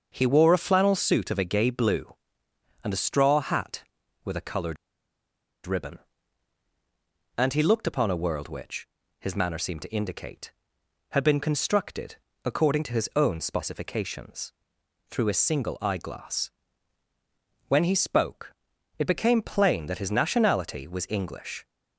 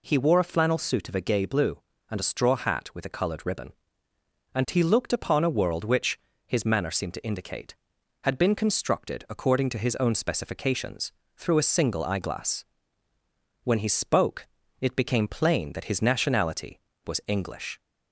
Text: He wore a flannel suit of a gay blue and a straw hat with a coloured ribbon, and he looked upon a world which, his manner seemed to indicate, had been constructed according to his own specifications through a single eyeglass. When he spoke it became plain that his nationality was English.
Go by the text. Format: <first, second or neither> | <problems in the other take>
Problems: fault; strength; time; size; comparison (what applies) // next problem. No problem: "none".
second | starts louder than the rest; until 1.1 s; 6.5 dB // pauses between "coloured" and "ribbon"; noticeable; at 4.7 s; 0.90 s long // pauses between "constructed" and "according"; slight; at 12.1 s; 0.28 s long // pauses between "specifications" and "through"; noticeable; at 14.5 s; 0.56 s long; slight in the second // pauses between "spoke" and "it"; noticeable; at 18.5 s; 0.46 s long; slight in the second